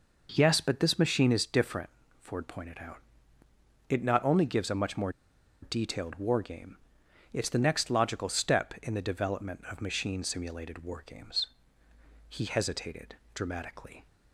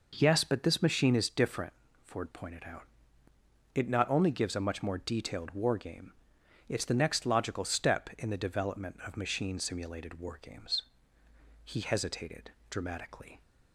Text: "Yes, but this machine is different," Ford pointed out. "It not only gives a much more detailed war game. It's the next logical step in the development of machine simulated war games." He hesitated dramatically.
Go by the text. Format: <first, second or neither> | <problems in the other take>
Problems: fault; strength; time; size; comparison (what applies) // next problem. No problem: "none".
second | pauses between "more" and "detailed"; noticeable; at 5.1 s; 0.51 s long // pauses between "hesitated" and "dramatically"; slight; at 13.1 s; 0.18 s long; slight in the second